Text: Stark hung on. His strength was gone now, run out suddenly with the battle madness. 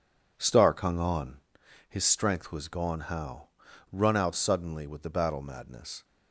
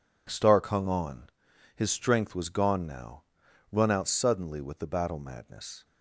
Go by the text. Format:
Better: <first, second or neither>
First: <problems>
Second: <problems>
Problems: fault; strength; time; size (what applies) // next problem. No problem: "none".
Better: second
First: says "how" for "now"; at 3.0 s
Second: none